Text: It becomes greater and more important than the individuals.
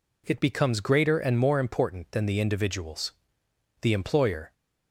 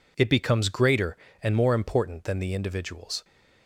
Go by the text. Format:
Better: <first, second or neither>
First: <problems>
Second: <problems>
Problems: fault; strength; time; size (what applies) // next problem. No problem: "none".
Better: second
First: goes on to say "The employer"; noticeable; from 3.8 s on; 0.70 s long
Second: none